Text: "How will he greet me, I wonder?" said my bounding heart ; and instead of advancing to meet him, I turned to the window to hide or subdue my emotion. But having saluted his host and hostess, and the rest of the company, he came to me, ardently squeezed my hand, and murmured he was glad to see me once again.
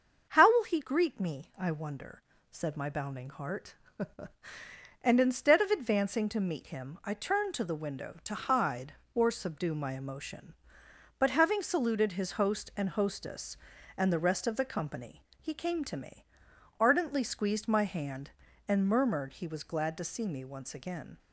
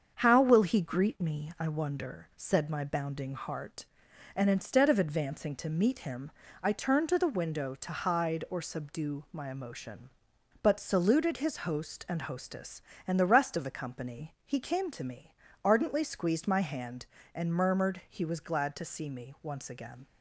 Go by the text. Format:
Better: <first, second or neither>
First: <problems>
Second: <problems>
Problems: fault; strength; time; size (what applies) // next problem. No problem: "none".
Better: first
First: starts louder than the rest; until 1.3 s; 6.5 dB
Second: starts louder than the rest; until 1.1 s; 7 dB // skips "having"; at 10.7 s